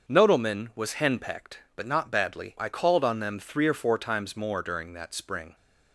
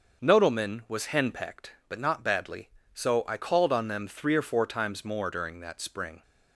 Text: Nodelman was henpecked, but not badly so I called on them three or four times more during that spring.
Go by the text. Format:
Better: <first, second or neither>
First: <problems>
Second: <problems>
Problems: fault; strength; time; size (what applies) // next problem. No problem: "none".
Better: second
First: starts louder than the rest; until 1.1 s; 6.5 dB // skips "so"; at 2.5 s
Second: starts louder than the rest; noticeable; until 1.2 s; 6 dB